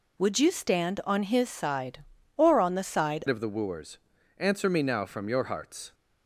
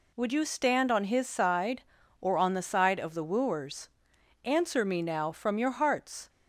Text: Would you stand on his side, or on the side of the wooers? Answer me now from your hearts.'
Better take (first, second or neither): second